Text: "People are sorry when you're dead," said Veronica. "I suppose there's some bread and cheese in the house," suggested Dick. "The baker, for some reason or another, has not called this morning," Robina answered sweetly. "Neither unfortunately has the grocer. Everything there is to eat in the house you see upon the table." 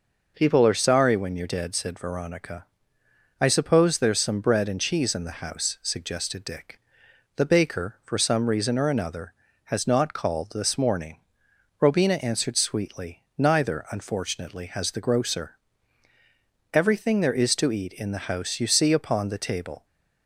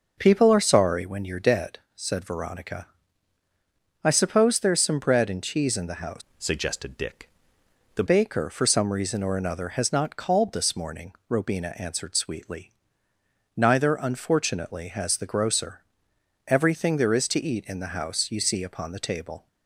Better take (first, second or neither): first